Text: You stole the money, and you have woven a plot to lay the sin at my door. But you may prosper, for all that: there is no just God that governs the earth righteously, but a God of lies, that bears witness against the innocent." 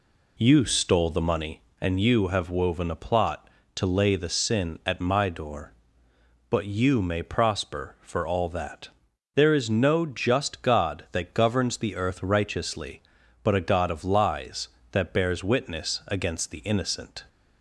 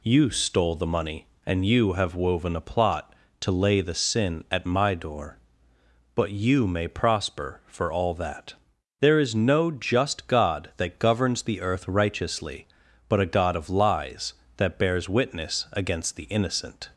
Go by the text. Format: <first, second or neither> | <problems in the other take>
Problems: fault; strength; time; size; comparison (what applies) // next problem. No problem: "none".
second | starts louder than the rest; slight; until 1.6 s; 2 dB